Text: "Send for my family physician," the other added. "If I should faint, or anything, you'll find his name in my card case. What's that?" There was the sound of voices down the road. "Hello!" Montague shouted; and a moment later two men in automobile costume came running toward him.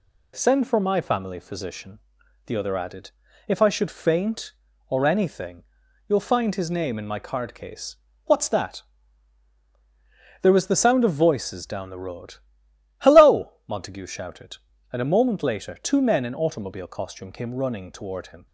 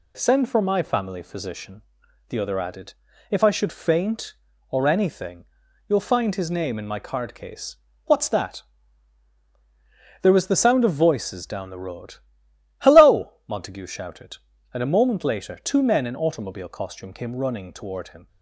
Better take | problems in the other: neither | none

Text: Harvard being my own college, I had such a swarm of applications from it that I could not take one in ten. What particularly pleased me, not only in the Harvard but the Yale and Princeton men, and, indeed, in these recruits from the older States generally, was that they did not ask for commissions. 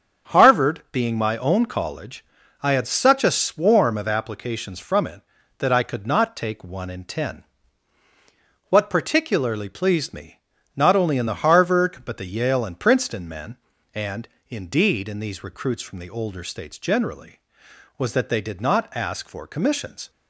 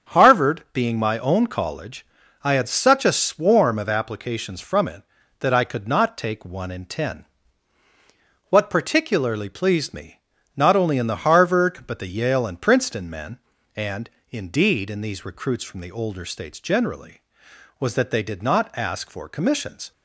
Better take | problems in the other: neither | starts louder than the rest; strong; the same in both

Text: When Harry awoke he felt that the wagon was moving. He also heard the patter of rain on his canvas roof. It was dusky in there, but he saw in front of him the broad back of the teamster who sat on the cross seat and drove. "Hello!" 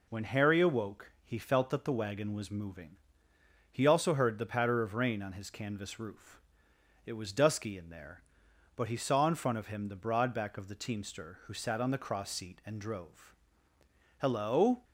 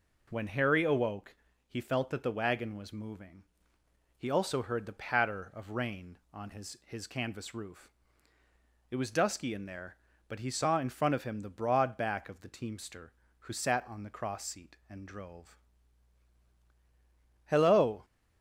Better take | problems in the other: first | pauses between "awoke" and "he"; slight; at 1.3 s; 0.36 s long // says "his" twice; at 6.8 s

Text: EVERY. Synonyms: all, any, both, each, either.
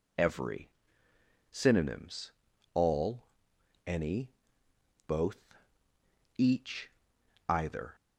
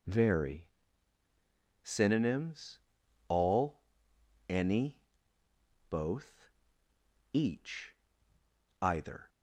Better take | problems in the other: first | says "Very" for "EVERY"; at 0.0 s

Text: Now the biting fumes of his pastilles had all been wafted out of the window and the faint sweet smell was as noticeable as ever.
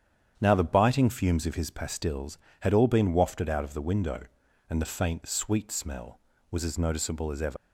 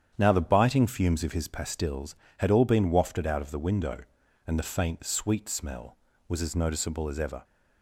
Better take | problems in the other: second | starts louder than the rest; strong; until 1.4 s; 9 dB; strong in the second // leaves "ever" unfinished; at 7.5 s; 95 ms

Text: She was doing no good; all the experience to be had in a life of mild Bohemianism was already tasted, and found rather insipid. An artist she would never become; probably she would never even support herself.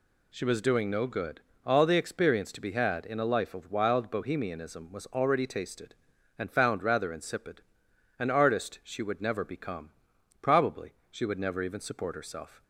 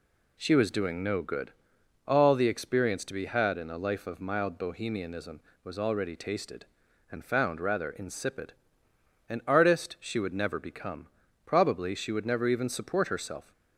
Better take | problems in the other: second | says "wild" for "mild"; at 3.7 s // pauses between "probably" and "she"; slight; at 10.9 s; 0.16 s long

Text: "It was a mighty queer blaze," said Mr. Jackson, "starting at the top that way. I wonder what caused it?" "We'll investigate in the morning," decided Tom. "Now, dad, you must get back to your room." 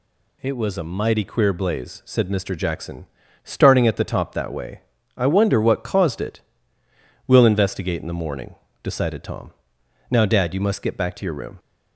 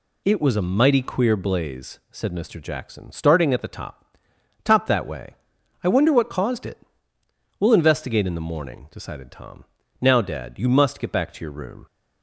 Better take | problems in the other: first | says "top" twice; at 4.6 s

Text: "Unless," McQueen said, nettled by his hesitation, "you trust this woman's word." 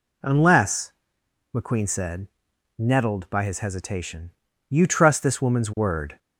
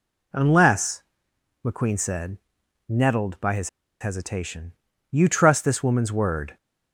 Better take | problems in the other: first | pauses between "his" and "hesitation"; slight; at 3.6 s; 0.31 s long

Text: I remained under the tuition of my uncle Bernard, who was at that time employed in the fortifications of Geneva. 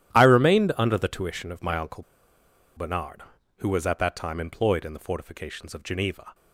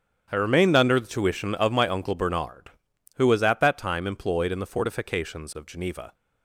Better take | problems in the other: second | starts louder than the rest; strong; until 1.1 s; 11.5 dB; strong in the second // pauses between "uncle" and "Bernard"; noticeable; at 2.0 s; 0.73 s long

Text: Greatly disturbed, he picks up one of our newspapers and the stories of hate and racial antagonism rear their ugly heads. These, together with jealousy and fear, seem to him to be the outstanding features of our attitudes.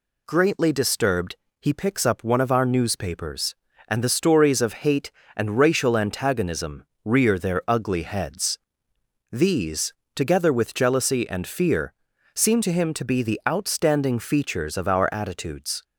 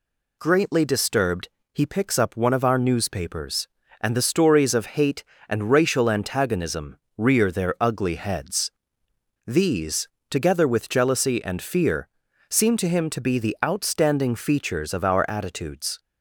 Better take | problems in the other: neither | pauses between "antagonism" and "rear"; slight; the same in both

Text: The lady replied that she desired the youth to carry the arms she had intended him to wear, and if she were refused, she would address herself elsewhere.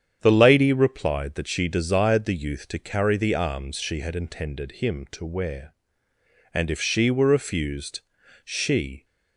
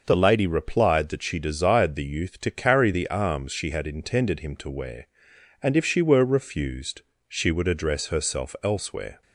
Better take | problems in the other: second | starts louder than the rest; strong; until 1.2 s; 8.5 dB // stops before "would address herself elsewhere"; at 9.0 s

